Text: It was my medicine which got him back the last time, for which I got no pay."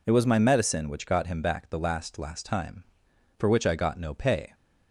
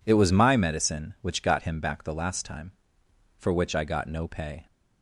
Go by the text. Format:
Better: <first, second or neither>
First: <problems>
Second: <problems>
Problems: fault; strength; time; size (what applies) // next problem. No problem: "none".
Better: second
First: says "last" twice; at 2.1 s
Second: none